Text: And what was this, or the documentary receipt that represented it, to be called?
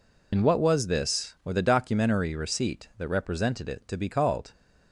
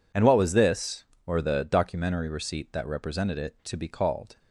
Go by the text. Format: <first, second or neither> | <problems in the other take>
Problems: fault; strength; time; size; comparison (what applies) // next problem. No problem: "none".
second | loses the start of "And"; at 0.3 s; 30 ms